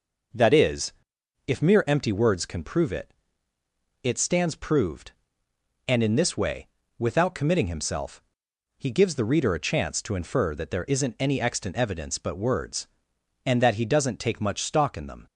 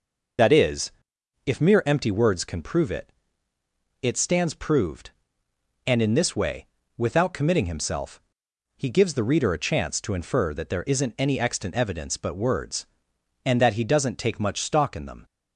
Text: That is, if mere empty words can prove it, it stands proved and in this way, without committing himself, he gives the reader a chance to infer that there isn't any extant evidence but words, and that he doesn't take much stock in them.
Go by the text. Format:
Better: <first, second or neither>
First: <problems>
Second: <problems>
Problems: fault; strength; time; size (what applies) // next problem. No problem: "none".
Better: first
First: none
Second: loses the start of "That"; at 0.3 s; 75 ms